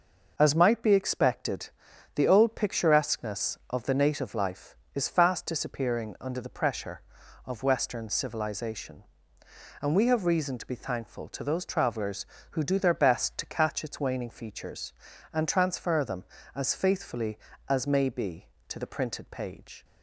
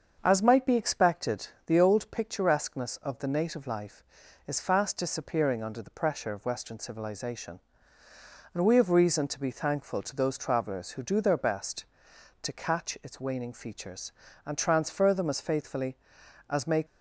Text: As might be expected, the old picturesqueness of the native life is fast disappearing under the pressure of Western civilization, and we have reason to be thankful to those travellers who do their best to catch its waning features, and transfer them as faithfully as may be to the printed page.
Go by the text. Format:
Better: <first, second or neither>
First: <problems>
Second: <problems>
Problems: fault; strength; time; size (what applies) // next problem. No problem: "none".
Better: first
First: none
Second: starts louder than the rest; until 1.2 s; 6.5 dB // stops before "be to the printed page"; at 16.8 s